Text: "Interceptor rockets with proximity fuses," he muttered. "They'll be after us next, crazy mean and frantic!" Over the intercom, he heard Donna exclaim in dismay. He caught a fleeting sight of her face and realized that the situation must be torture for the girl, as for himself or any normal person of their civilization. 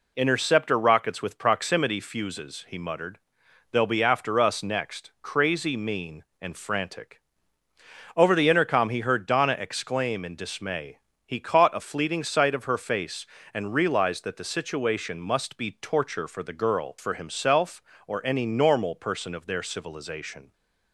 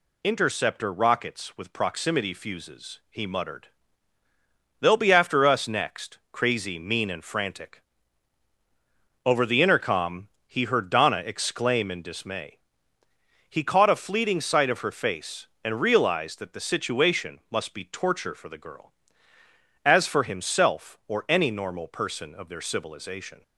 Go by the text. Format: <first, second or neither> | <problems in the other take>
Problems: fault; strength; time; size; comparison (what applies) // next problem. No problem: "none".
second | skips "as"; at 16.9 s